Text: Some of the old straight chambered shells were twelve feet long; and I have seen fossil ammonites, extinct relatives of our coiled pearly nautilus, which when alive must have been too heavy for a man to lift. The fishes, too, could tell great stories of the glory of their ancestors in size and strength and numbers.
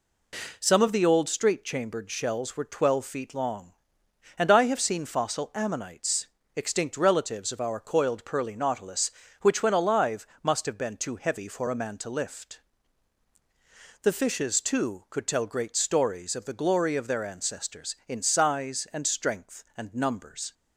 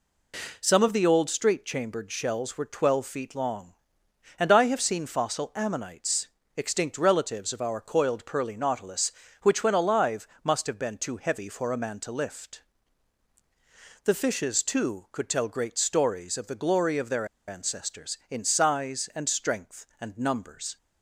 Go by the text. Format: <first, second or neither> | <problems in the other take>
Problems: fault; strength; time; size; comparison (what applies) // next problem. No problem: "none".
first | pauses between "alive" and "must"; slight; at 10.2 s; 0.16 s long; slight in the first // pauses between "their" and "ancestors"; slight; at 17.2 s; 0.22 s long